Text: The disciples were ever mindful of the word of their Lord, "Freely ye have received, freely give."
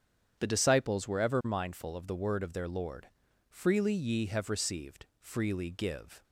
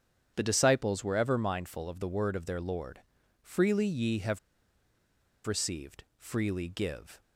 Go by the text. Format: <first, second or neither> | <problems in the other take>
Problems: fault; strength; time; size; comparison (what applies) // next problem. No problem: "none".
first | starts louder than the rest; strong; until 1.3 s; 8.5 dB; strong in the first // pauses between "have" and "received"; at 4.3 s; 1.0 s long